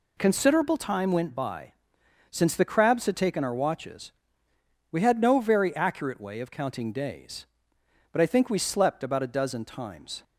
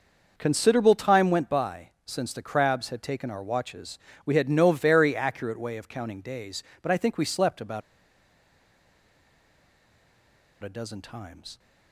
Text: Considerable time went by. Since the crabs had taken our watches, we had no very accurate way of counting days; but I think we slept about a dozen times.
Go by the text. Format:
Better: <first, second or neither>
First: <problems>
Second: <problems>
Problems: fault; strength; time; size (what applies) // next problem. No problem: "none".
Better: first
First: none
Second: starts louder than the rest; noticeable; until 1.3 s; 6 dB // pauses between "about" and "a"; strong; at 7.8 s; 2.8 s long